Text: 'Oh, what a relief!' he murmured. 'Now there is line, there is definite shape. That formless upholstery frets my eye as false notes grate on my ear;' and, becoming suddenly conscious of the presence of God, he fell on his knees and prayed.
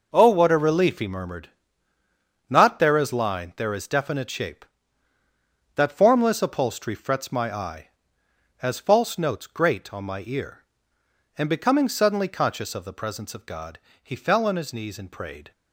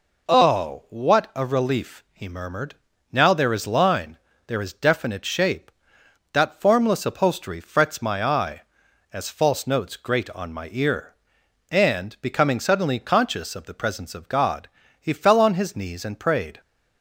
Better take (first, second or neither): second